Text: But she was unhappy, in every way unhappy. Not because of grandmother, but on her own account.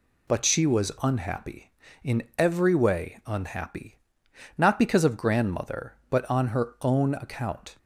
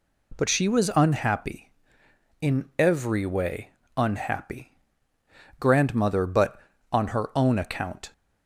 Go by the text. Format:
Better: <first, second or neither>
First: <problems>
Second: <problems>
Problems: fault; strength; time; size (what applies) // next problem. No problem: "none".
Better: first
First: none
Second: pauses between "way" and "unhappy"; slight; at 3.7 s; 0.26 s long // skips "Not because of"; at 5.1 s